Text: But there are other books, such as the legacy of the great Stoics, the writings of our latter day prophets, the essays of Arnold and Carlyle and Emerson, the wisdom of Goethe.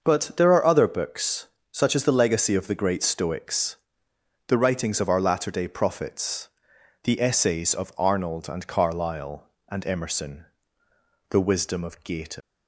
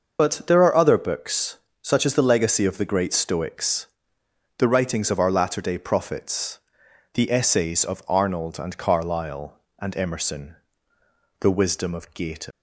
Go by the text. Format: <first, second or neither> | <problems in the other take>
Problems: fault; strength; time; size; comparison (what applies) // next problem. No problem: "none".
first | loses the start of "But"; at 0.1 s; 55 ms